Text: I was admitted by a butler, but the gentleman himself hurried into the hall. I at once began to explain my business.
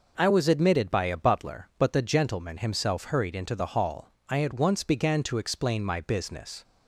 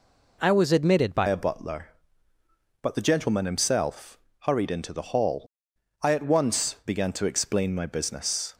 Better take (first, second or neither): first